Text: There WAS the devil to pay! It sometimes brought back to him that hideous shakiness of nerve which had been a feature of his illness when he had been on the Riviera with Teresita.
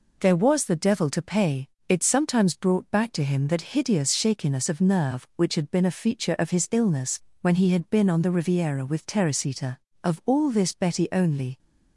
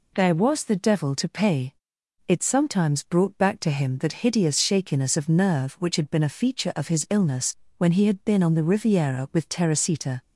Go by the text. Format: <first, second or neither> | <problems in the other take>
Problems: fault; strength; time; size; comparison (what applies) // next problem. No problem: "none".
second | pauses between "illness" and "when"; slight; at 7.2 s; 0.22 s long; slight in the second // goes on to say "Of all this Betty only"; from 10.0 s on; 1.5 s long